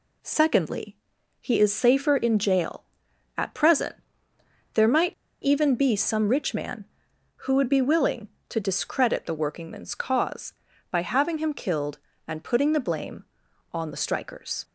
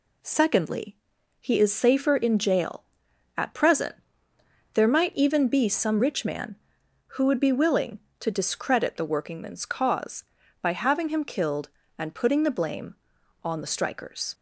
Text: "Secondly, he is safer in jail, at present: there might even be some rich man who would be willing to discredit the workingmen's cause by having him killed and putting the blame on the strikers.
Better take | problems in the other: second | pauses between "might" and "even"; slight; at 5.1 s; 0.29 s long

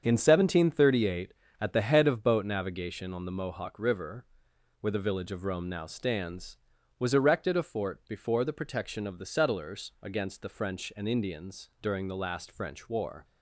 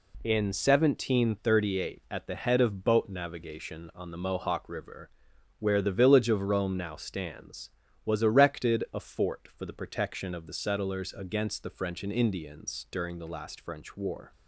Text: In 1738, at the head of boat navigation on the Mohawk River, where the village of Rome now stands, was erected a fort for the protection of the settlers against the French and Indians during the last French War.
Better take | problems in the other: second | starts louder than the rest; strong; until 1.0 s; 7.5 dB // says "before" for "for"; at 8.0 s

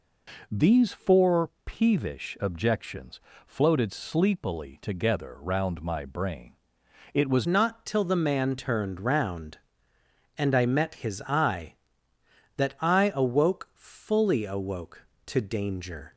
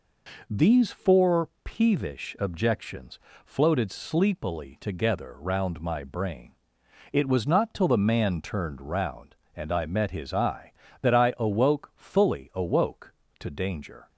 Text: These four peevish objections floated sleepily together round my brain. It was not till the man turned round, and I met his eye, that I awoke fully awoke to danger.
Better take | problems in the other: second | pauses between "four" and "peevish"; slight; at 1.4 s; 0.16 s long; slight in the second // pauses between "objections" and "floated"; slight; at 3.1 s; 0.28 s long; slight in the second // changes voice at "not"; from 7.4 s on; 8.7 s long

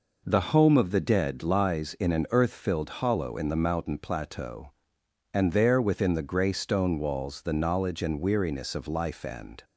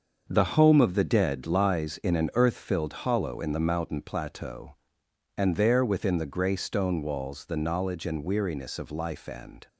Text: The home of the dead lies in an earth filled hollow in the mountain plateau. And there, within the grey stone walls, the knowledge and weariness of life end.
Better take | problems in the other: first | gets quieter; strong; throughout; 8.5 dB

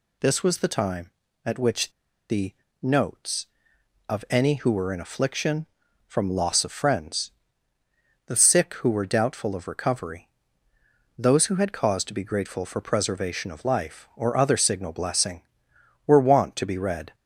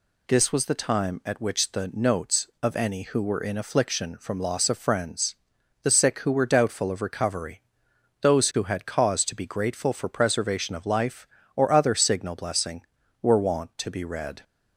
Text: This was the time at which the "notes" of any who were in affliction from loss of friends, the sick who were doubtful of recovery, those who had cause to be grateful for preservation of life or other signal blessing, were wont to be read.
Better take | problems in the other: second | pauses between "which" and "the"; at 1.9 s; 0.39 s long // pauses between "the" and "notes"; slight; at 2.5 s; 0.26 s long

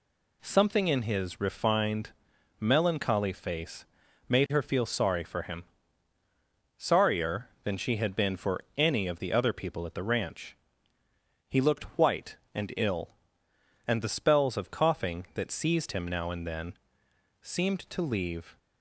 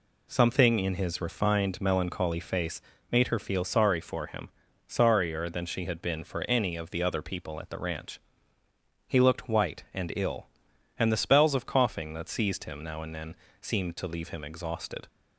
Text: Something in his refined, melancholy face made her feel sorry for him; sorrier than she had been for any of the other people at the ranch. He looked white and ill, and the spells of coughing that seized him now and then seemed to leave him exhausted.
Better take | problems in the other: second | pauses between "face" and "made"; at 3.8 s; 0.42 s long; slight in the second // pauses between "for" and "any"; slight; at 8.5 s; 0.16 s long // pauses between "then" and "seemed"; noticeable; at 16.7 s; 0.64 s long; slight in the second // stops before "him exhausted"; at 18.5 s

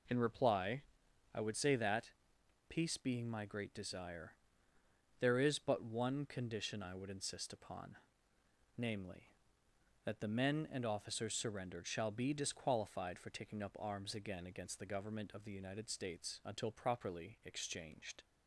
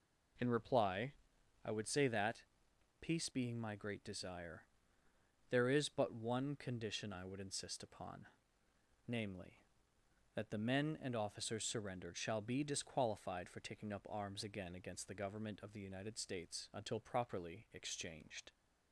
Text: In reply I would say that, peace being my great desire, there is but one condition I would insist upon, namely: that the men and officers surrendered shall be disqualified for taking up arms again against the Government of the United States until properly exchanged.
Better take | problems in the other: neither | pauses between "reply" and "I"; noticeable; the same in both

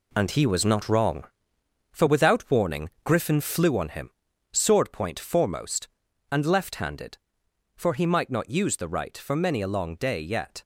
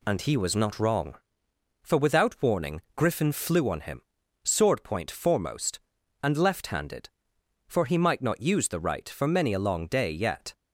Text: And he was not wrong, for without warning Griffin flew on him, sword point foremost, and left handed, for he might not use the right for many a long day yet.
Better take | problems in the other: second | gets quieter; strong; throughout; 8.5 dB // pauses between "warning" and "Griffin"; slight; at 2.8 s; 0.16 s long; slight in the second

